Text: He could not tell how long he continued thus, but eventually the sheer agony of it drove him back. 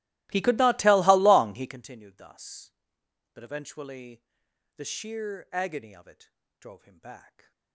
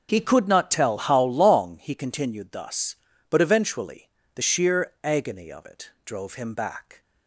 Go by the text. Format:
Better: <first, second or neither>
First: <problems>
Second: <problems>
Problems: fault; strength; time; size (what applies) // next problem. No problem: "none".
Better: second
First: starts louder than the rest; strong; until 1.8 s; 17.5 dB // pauses between "eventually" and "the"; noticeable; at 4.2 s; 0.52 s long // pauses between "it" and "drove"; slight; at 6.2 s; 0.30 s long // stays silent after the last word; slight; from 7.2 s on; 0.5 s long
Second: pauses between "eventually" and "the"; slight; at 4.0 s; 0.24 s long // pauses between "it" and "drove"; slight; at 5.9 s; 0.16 s long